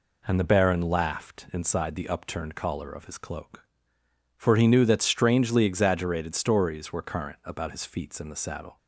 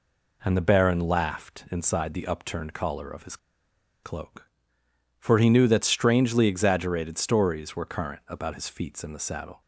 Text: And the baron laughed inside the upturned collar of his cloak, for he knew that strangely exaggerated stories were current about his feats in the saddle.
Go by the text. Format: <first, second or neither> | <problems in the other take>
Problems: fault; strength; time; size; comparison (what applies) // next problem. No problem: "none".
first | pauses between "his" and "cloak"; noticeable; at 3.3 s; 0.66 s long